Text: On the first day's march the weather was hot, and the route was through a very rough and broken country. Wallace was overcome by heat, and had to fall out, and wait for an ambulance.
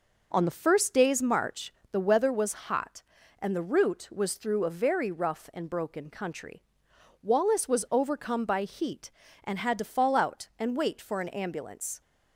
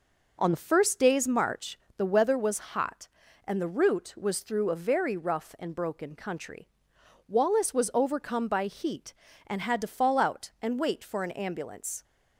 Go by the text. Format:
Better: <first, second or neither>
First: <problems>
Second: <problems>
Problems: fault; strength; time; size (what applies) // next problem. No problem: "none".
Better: neither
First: pauses between "march" and "the"; slight; at 1.7 s; 0.18 s long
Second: pauses between "march" and "the"; slight; at 1.7 s; 0.18 s long